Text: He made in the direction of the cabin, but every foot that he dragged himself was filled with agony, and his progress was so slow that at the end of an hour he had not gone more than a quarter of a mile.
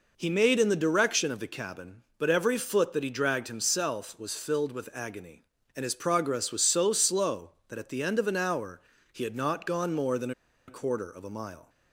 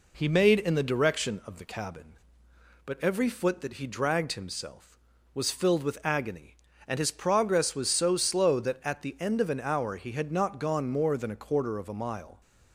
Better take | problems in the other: second | pauses between "hour" and "he"; slight; at 8.7 s; 0.32 s long // pauses between "than" and "a"; at 10.3 s; 0.36 s long

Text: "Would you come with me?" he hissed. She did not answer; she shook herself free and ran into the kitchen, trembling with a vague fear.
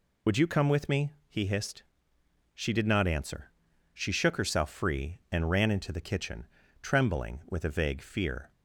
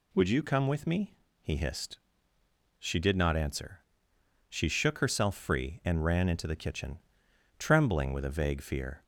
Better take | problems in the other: second | loses the start of "Would"; at 0.2 s; 65 ms

